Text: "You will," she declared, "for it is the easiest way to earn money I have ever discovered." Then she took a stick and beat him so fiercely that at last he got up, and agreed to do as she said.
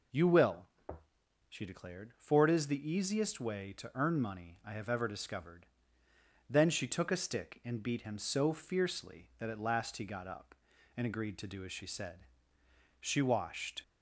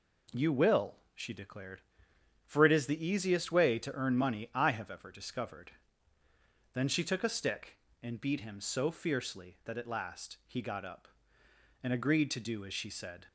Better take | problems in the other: second | goes on to say "She washed"; noticeable; from 13.0 s on; 0.82 s long

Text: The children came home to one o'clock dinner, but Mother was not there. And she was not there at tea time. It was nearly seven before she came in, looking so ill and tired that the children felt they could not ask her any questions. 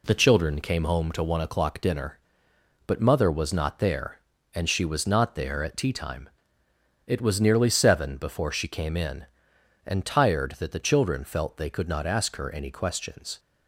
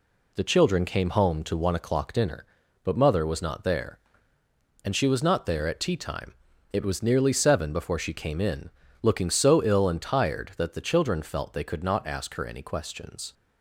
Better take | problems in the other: second | skips "looking so ill"; at 9.5 s

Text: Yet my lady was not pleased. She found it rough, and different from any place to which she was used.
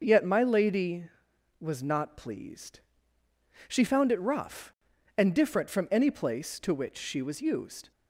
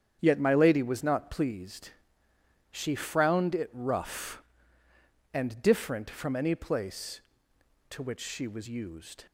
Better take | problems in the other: first | starts louder than the rest; strong; until 1.2 s; 8.5 dB // says "frowned" for "found"; at 2.9 s

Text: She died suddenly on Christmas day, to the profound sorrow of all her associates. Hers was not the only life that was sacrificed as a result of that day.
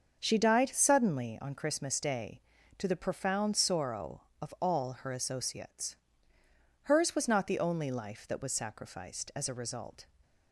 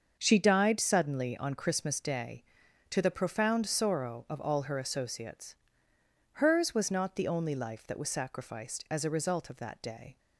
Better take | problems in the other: second | starts louder than the rest; until 1.2 s; 6.5 dB; also in the second // stops before "of that day"; at 10.2 s

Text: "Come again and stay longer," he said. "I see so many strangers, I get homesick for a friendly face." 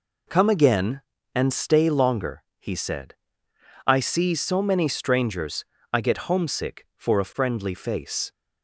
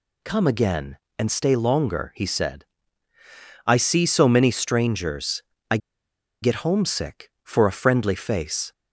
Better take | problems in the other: first | pauses between "I" and "get"; noticeable; at 5.7 s; 0.64 s long

